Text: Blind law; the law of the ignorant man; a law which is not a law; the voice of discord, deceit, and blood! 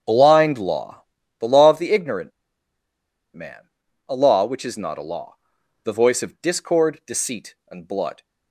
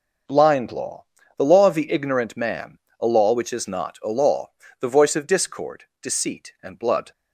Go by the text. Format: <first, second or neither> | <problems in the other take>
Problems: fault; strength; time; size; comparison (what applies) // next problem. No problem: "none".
second | starts louder than the rest; strong; until 1.4 s; 7.5 dB // pauses between "ignorant" and "man"; at 2.3 s; 1.0 s long